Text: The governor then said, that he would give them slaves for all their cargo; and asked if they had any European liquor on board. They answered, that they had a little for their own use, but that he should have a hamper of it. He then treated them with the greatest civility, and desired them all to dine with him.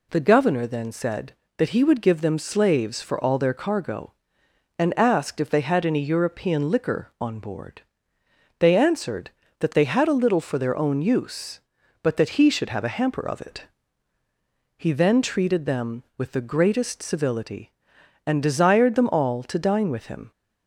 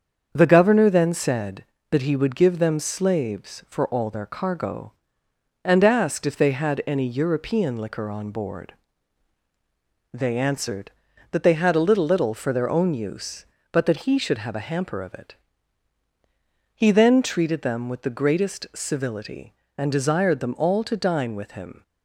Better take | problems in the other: first | starts louder than the rest; strong; until 1.3 s; 7 dB // says "little" twice; at 12.0 s

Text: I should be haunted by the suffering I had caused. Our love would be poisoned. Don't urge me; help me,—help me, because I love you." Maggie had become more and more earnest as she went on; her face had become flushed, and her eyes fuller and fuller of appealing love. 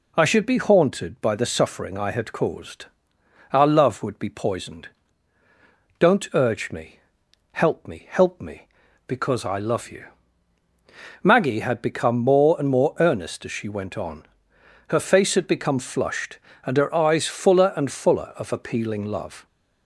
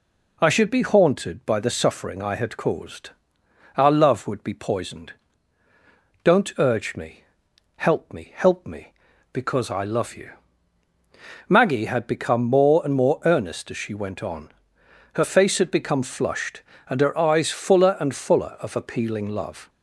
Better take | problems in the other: neither | none

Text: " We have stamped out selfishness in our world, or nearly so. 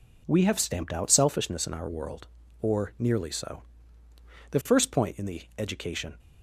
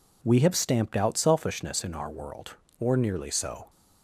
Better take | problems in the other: second | goes on to say "The first point in the education"; strong; from 4.4 s on; 1.6 s long

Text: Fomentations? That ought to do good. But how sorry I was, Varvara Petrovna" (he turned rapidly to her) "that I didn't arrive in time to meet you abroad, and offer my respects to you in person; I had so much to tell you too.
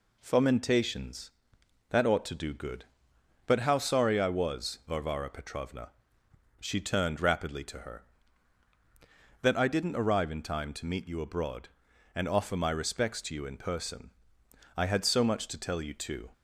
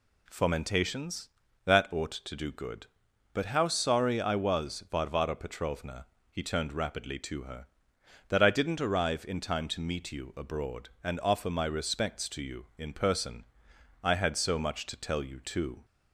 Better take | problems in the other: second | says "she" for "he"; at 6.6 s

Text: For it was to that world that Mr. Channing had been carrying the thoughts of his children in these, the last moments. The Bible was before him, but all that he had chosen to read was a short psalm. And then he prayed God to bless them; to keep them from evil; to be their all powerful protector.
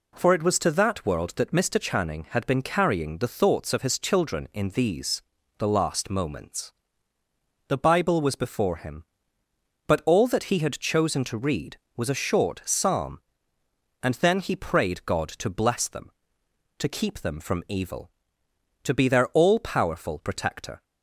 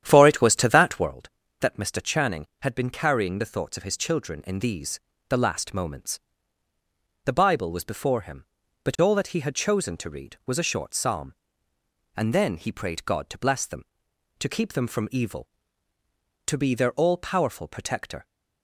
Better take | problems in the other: first | starts louder than the rest; strong; until 1.1 s; 10 dB

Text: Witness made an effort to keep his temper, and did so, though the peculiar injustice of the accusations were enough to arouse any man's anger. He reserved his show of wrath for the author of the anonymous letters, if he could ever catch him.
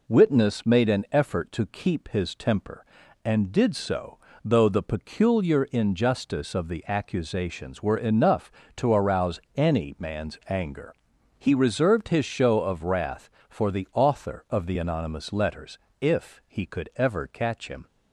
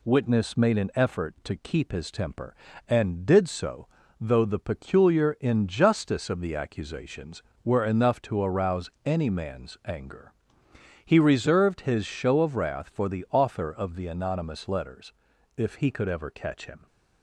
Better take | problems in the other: neither | pauses between "arouse" and "any"; slight; the same in both

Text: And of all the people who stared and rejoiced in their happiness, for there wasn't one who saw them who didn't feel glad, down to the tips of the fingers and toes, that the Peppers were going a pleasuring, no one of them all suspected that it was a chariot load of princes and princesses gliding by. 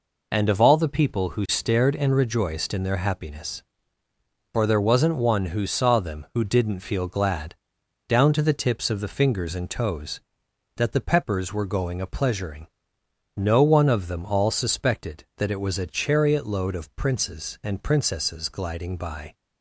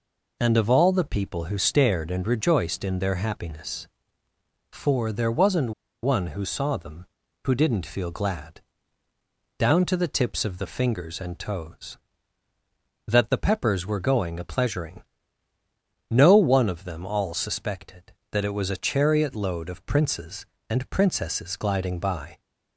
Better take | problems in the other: first | pauses between "wasn't" and "one"; slight; at 5.7 s; 0.31 s long

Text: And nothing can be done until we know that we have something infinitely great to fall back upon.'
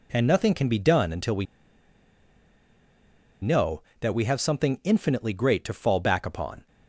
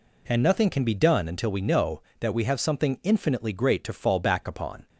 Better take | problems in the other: second | pauses between "we" and "know"; strong; at 1.4 s; 1.9 s long

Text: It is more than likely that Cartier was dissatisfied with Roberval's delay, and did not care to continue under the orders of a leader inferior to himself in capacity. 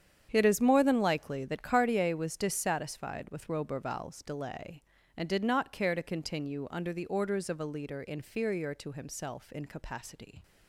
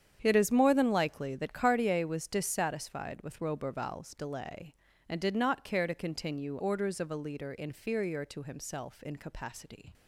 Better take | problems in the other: first | starts louder than the rest; strong; until 1.2 s; 8.5 dB; strong in the first // skips "under the"; at 6.6 s

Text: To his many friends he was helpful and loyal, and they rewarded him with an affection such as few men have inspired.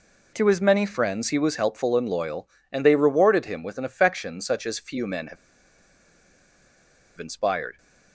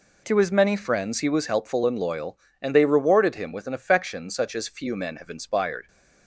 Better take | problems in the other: second | pauses between "have" and "inspired"; strong; at 5.3 s; 1.8 s long

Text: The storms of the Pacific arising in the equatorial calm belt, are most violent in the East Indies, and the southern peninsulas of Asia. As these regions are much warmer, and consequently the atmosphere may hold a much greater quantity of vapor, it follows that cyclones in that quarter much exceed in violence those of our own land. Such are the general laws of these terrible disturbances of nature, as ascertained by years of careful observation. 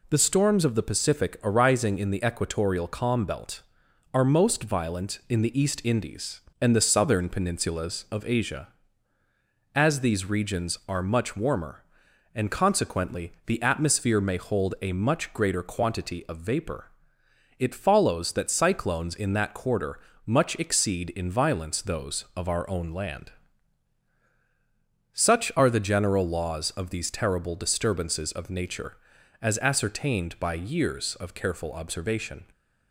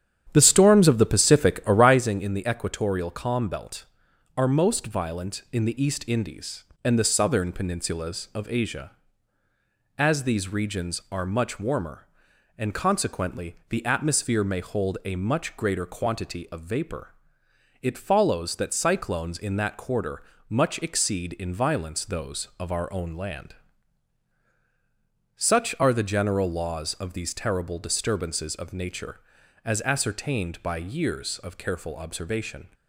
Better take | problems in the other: first | starts louder than the rest; strong; until 2.1 s; 9.5 dB // pauses between "quarter" and "much"; slight; at 20.2 s; 0.28 s long; slight in the first

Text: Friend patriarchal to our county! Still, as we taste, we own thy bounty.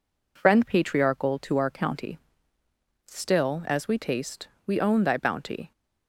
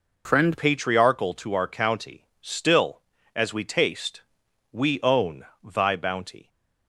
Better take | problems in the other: first | changes voice at "patriarchal"; from 0.5 s on; 5.9 s long // pauses between "own" and "thy"; slight; at 5.4 s; 0.18 s long

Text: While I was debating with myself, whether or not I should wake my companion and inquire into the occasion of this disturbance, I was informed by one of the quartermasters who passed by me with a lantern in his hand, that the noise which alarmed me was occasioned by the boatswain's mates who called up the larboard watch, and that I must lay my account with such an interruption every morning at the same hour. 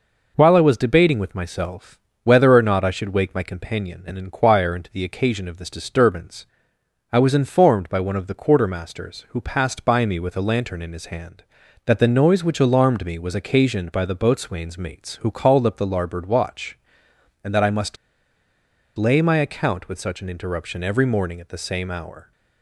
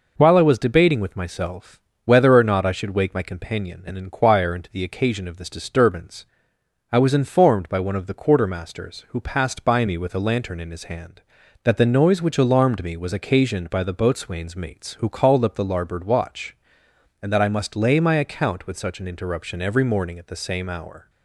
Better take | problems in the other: second | pauses between "must" and "lay"; at 17.9 s; 1.0 s long

